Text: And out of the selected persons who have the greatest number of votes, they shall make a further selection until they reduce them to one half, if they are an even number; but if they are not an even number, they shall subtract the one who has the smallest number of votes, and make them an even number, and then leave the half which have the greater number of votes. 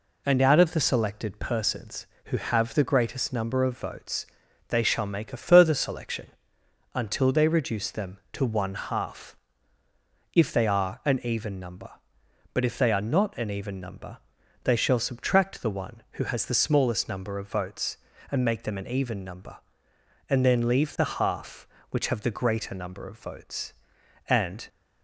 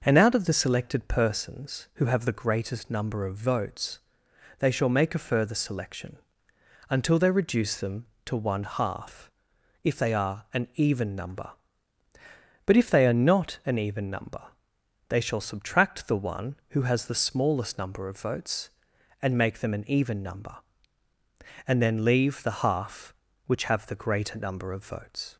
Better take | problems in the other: second | pauses between "selection" and "until"; noticeable; at 6.2 s; 0.68 s long; noticeable in the second // goes on to say "And"; slight; from 24.2 s on; 0.40 s long

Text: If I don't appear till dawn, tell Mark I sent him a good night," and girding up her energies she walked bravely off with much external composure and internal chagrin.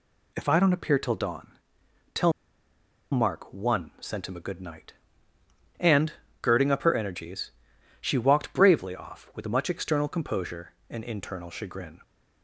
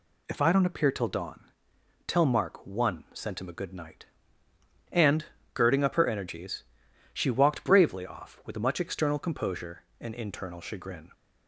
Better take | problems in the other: second | pauses between "tell" and "Mark"; noticeable; at 2.3 s; 0.80 s long // pauses between "and" and "girding"; slight; at 6.1 s; 0.26 s long; slight in the second // pauses between "energies" and "she"; noticeable; at 7.5 s; 0.50 s long; noticeable in the second

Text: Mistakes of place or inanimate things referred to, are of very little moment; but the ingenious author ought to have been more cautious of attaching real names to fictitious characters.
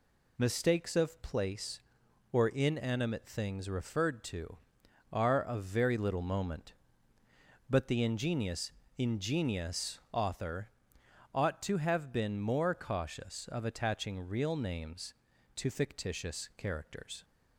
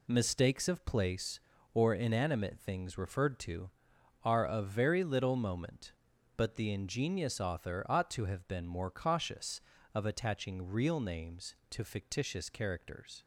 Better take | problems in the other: second | says "ingenious" twice; at 8.9 s // pauses between "author" and "ought"; noticeable; at 10.6 s; 0.66 s long

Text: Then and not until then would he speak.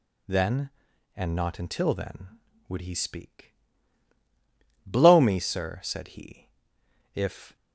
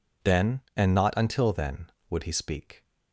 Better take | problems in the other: second | goes on to say "Blow me sir said he if"; strong; from 4.8 s on; 2.7 s long

